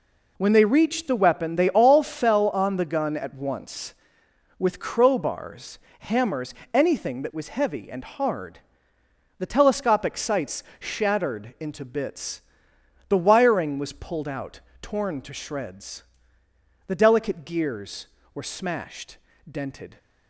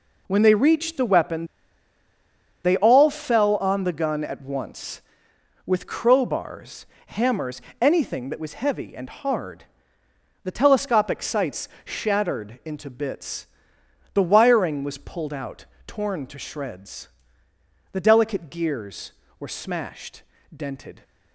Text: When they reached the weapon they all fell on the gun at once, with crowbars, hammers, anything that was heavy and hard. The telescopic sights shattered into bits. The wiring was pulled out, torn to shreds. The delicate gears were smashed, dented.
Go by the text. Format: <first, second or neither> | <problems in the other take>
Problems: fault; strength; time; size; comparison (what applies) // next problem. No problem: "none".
first | pauses between "weapon" and "they"; at 1.4 s; 1.1 s long // pauses between "sights" and "shattered"; slight; at 11.6 s; 0.16 s long; slight in the first